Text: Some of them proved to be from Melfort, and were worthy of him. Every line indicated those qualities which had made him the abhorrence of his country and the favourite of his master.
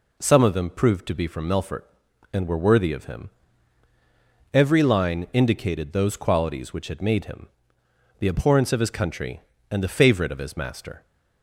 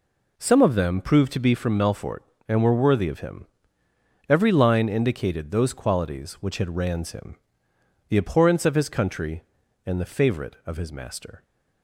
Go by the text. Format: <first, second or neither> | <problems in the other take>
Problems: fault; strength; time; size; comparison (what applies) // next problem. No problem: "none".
first | says "rans" for "made"; at 6.7 s // pauses between "him" and "the"; noticeable; at 7.3 s; 0.70 s long; noticeable in the first